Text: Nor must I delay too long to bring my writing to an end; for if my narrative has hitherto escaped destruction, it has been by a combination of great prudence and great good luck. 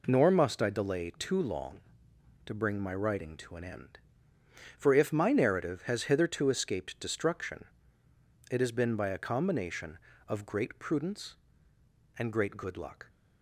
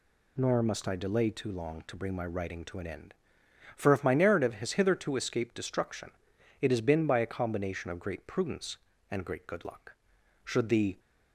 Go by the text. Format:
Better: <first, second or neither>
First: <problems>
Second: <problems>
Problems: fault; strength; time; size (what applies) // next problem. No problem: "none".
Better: first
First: none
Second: goes on to say "Should the"; from 10.4 s on; 0.54 s long